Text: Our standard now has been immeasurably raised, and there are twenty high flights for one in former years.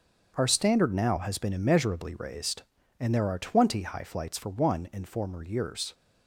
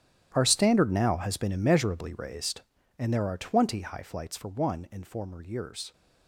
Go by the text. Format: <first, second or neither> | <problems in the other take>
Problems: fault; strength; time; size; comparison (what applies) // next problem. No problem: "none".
first | gets quieter; strong; throughout; 17 dB // starts louder than the rest; strong; until 1.3 s; 11 dB; also in the first